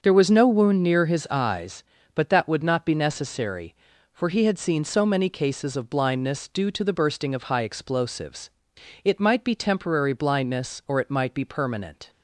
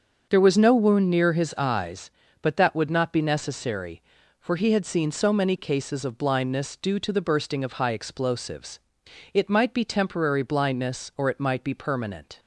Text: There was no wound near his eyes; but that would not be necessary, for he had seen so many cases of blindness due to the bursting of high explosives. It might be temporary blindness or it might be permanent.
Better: neither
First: starts louder than the rest; until 1.0 s; 6 dB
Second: starts louder than the rest; until 1.3 s; 6.5 dB

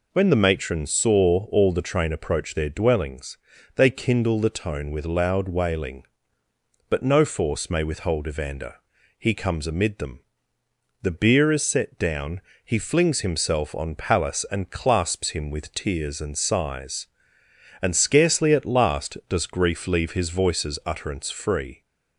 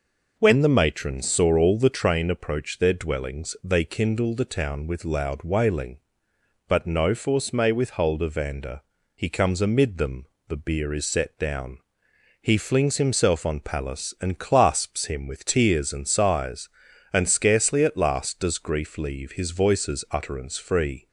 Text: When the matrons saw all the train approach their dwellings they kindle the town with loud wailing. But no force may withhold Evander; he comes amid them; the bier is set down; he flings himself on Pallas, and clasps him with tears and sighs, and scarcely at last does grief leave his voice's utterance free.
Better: second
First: pauses between "dwellings" and "they"; at 3.3 s; 0.40 s long // says "tone" for "town"; at 4.4 s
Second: none

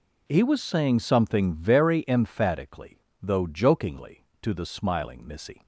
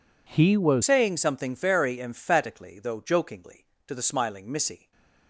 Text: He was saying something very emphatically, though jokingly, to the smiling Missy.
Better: first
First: none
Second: changes voice at "saying"; from 0.8 s on; 4.1 s long // stays silent after the last word; slight; from 4.7 s on; 0.5 s long

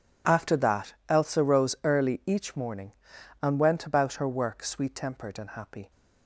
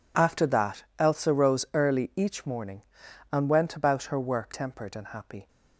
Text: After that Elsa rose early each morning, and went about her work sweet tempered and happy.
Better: first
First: none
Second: skips "sweet"; at 4.5 s

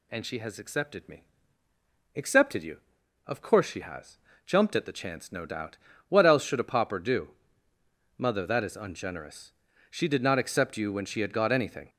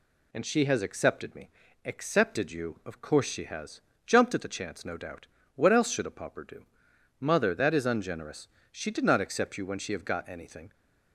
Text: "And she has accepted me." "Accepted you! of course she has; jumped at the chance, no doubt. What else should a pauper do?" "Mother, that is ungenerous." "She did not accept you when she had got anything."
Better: first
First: none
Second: says "have" for "had"; at 9.9 s

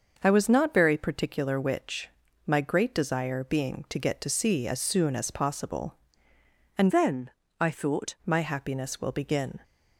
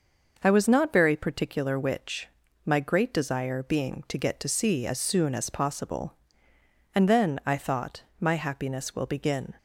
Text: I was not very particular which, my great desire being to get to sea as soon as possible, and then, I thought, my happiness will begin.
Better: second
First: starts louder than the rest; until 1.2 s; 6 dB // changes voice from "then" to "thought"; from 6.9 to 8.1 s; 1.2 s long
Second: none

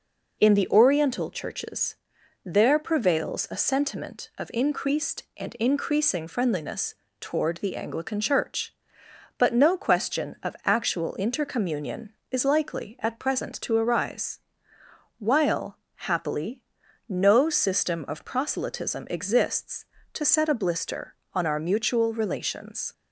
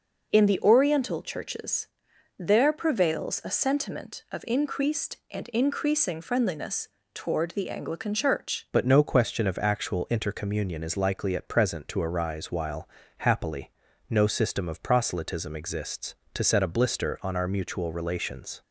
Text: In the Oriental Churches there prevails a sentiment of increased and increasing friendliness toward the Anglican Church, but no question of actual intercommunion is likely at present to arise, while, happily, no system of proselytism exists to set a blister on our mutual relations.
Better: first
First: pauses between "Churches" and "there"; noticeable; at 1.9 s; 0.48 s long // pauses between "friendliness" and "toward"; slight; at 6.9 s; 0.28 s long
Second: pauses between "Churches" and "there"; noticeable; at 1.8 s; 0.50 s long // pauses between "friendliness" and "toward"; slight; at 6.8 s; 0.28 s long // changes voice at "but"; from 8.7 s on; 9.9 s long

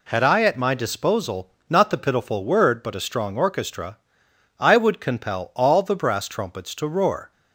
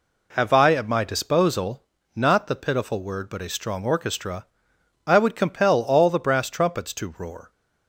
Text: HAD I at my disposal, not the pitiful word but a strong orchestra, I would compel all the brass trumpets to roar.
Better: first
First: none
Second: says "Have" for "HAD"; at 0.3 s

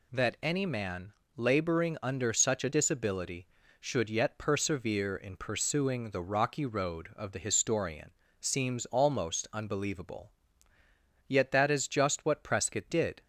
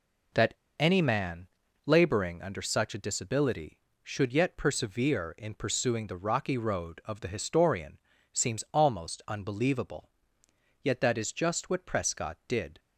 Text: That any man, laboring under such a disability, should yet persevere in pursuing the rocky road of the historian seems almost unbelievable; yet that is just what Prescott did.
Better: first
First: pauses between "historian" and "seems"; slight; at 8.1 s; 0.28 s long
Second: pauses between "That" and "any"; slight; at 0.5 s; 0.25 s long // pauses between "historian" and "seems"; slight; at 7.9 s; 0.32 s long

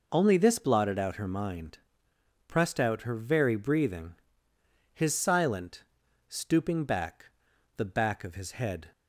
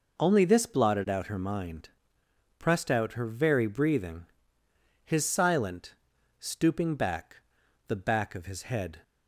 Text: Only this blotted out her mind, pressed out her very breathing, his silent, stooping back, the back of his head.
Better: neither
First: none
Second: none

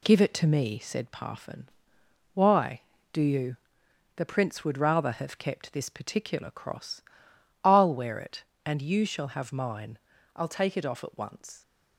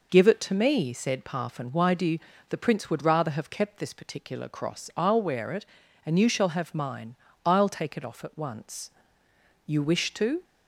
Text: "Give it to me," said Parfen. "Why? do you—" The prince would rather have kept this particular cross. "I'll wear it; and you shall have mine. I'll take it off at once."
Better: first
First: none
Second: goes on to say "You wish to"; noticeable; from 9.6 s on; 0.78 s long

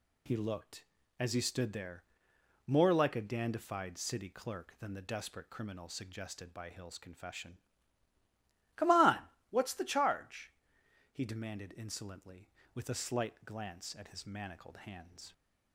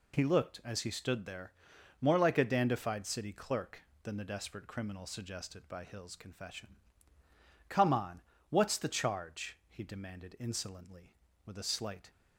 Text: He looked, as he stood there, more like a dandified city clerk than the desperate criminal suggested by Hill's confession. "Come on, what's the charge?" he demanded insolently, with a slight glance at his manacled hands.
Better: first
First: none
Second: stops before "glance at his manacled hands"; at 12.1 s

